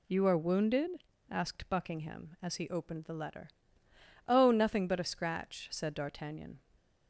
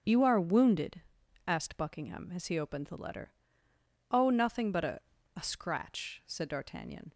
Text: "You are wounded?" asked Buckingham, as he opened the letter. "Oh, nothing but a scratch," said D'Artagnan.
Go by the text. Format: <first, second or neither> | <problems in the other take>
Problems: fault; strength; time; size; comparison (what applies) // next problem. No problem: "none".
first | starts louder than the rest; until 1.5 s; 6.5 dB // says "a" twice; at 5.3 s